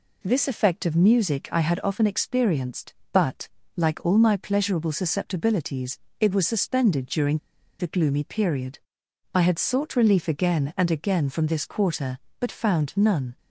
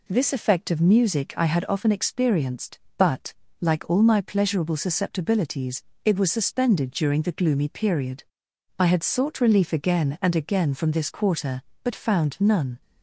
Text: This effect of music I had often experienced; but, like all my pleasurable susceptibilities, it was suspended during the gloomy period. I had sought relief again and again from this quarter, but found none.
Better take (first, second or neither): second